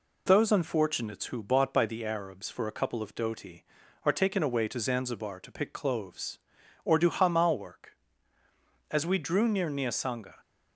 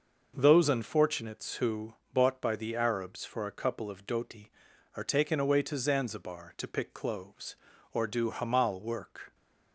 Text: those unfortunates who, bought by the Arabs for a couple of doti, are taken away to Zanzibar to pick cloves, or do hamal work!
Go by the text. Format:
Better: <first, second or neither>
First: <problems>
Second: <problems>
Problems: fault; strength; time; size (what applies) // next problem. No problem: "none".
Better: second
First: goes on to say "As we drew near Niasanga"; from 8.9 s on; 1.4 s long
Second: none